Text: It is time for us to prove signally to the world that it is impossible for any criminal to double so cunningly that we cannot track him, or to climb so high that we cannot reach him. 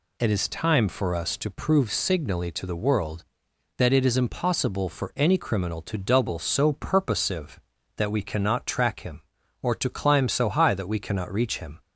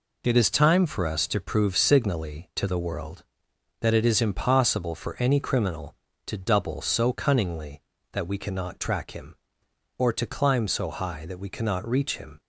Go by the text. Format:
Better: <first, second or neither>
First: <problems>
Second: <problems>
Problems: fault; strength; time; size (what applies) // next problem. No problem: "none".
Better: second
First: says "purposive" for "cunningly"; at 6.7 s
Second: none